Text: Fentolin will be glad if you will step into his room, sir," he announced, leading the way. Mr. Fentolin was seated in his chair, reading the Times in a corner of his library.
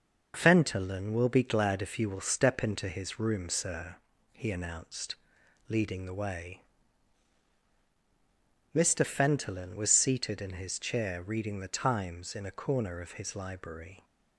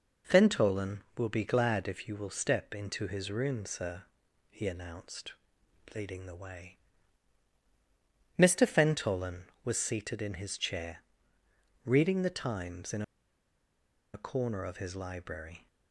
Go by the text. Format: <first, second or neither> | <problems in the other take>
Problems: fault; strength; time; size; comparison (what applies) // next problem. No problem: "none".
first | pauses between "in" and "a"; at 13.0 s; 1.1 s long